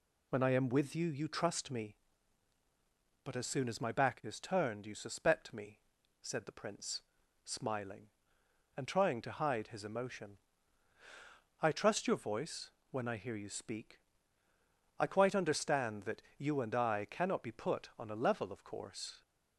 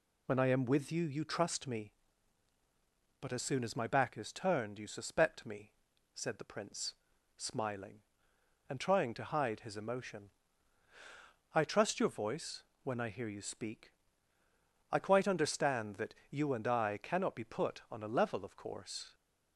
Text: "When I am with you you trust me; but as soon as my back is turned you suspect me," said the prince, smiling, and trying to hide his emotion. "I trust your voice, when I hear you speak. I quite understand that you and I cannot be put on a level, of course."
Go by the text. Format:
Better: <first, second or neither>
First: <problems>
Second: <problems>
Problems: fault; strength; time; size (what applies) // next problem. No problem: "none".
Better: neither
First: none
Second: none